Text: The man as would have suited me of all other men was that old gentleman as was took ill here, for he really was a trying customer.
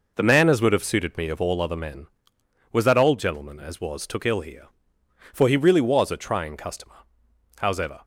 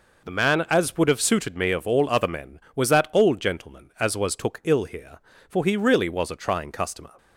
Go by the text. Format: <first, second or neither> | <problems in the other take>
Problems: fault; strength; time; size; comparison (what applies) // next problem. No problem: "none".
second | goes on to say "Howsever"; slight; from 7.5 s on; 0.46 s long